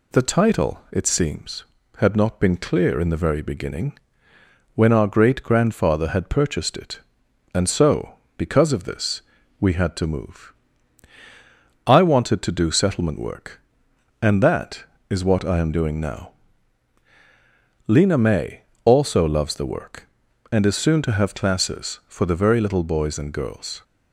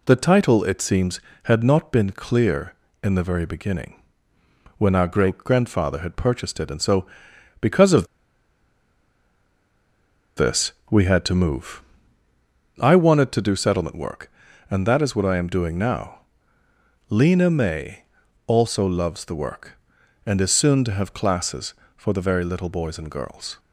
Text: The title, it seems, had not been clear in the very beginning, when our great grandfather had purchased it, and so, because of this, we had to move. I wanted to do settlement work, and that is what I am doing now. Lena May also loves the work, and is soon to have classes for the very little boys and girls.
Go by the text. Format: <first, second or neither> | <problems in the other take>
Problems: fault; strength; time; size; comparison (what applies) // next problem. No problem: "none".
first | pauses between "of" and "this"; strong; at 8.0 s; 2.3 s long // pauses between "May" and "also"; at 18.0 s; 0.42 s long; slight in the first